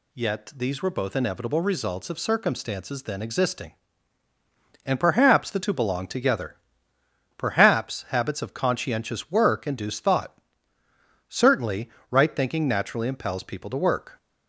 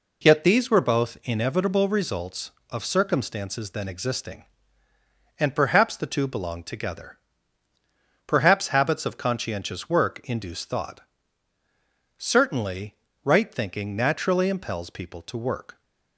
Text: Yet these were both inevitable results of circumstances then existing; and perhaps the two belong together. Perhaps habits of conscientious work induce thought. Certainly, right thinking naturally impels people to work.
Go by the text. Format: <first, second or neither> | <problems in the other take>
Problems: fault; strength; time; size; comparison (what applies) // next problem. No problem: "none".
neither | none